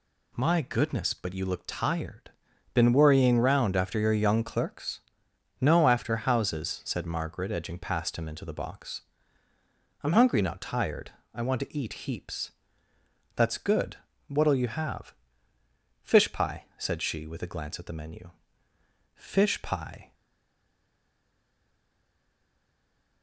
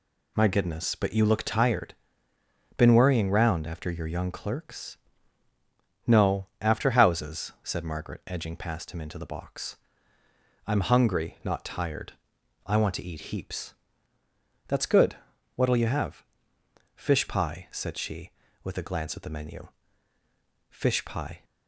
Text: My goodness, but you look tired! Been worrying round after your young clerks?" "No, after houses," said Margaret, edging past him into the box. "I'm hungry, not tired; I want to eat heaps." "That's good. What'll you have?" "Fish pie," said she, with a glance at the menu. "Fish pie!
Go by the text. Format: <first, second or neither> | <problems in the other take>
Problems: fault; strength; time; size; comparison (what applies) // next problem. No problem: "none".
second | stays silent after the last word; strong; from 20.1 s on; 3.1 s long